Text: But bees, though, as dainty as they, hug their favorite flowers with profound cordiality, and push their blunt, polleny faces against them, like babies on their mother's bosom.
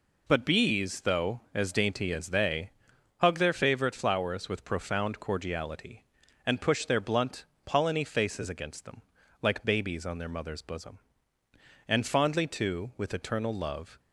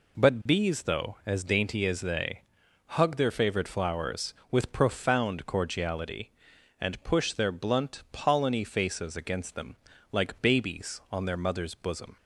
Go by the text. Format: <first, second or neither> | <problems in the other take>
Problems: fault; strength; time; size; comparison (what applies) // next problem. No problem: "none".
second | goes on to say "And fondly too with eternal love"; strong; from 11.8 s on; 2.1 s long